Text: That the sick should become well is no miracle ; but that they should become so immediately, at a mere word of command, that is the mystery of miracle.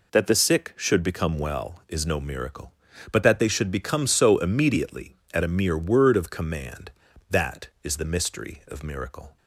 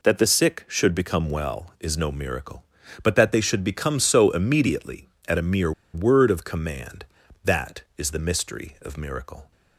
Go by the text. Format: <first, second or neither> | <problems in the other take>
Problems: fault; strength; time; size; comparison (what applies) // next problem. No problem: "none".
first | pauses between "mere" and "word"; slight; at 5.7 s; 0.22 s long